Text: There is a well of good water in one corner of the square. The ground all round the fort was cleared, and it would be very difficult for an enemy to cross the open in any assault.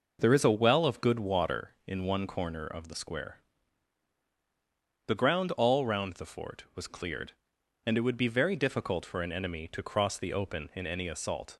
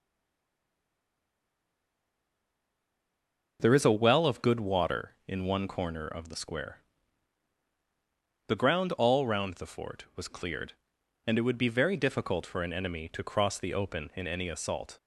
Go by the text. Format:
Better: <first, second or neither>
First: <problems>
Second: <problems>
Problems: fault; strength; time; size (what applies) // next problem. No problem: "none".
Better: first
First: none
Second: stays silent before the first word; strong; until 3.5 s; 3.5 s long